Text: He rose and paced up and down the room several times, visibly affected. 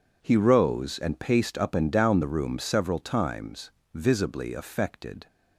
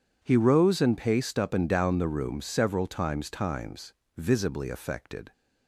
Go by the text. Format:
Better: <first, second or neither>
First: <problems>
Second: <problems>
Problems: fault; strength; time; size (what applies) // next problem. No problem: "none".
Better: first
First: none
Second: says "times" twice; at 3.2 s